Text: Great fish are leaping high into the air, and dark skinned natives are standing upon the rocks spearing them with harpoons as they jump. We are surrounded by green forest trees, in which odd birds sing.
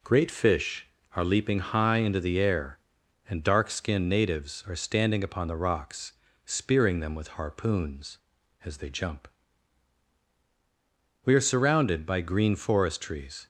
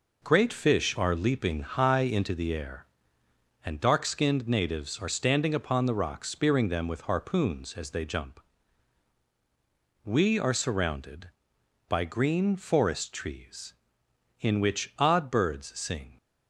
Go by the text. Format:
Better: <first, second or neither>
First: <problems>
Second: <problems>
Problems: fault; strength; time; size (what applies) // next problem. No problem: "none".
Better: second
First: pauses between "rocks" and "spearing"; slight; at 6.1 s; 0.32 s long // stops before "in which odd birds sing"; at 13.4 s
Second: none